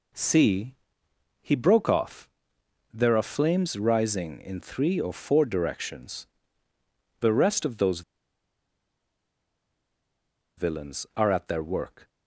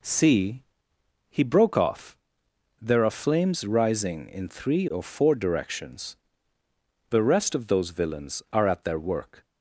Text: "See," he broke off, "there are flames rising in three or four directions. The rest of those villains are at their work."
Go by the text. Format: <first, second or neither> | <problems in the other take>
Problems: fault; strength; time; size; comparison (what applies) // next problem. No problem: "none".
second | pauses between "those" and "villains"; strong; at 8.0 s; 2.5 s long